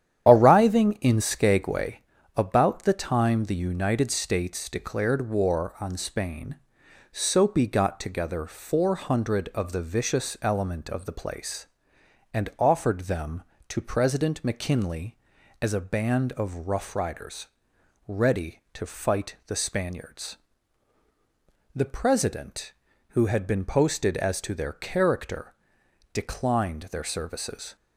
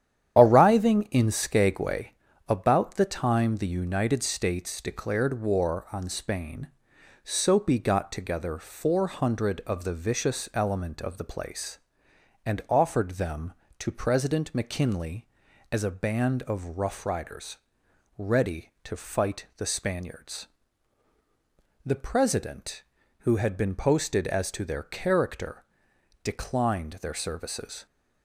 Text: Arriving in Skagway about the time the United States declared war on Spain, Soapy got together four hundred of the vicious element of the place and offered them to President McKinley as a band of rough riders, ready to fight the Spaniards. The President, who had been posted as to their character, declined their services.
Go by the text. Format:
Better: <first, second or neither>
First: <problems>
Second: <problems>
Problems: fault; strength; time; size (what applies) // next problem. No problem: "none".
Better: neither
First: starts louder than the rest; strong; until 1.3 s; 9 dB // pauses between "Skagway" and "about"; slight; at 1.9 s; 0.36 s long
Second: starts louder than the rest; strong; until 1.4 s; 9 dB // pauses between "Skagway" and "about"; slight; at 2.1 s; 0.36 s long